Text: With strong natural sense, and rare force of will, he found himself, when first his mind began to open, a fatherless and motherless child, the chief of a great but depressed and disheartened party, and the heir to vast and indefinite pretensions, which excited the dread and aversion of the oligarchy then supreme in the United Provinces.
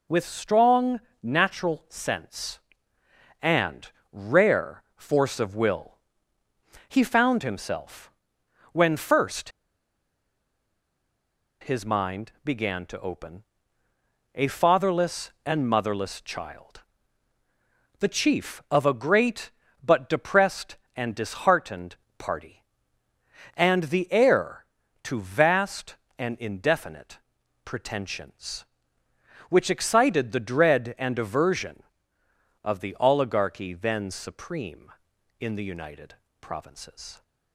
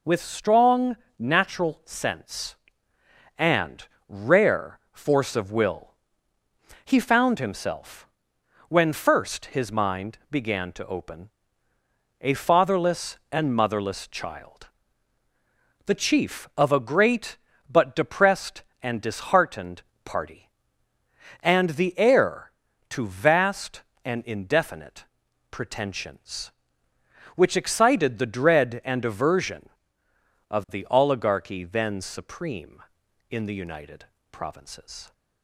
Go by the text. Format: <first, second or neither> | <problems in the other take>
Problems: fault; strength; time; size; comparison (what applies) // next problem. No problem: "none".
second | pauses between "strong" and "natural"; slight; at 0.9 s; 0.22 s long; slight in the second // pauses between "and" and "rare"; slight; at 3.9 s; 0.18 s long; slight in the second // pauses between "first" and "his"; strong; at 9.4 s; 2.1 s long // pauses between "disheartened" and "party"; slight; at 21.9 s; 0.24 s long; slight in the second // pauses between "indefinite" and "pretensions"; noticeable; at 27.1 s; 0.46 s long; noticeable in the second // pauses between "United" and "Provinces"; slight; at 36.1 s; 0.24 s long; slight in the second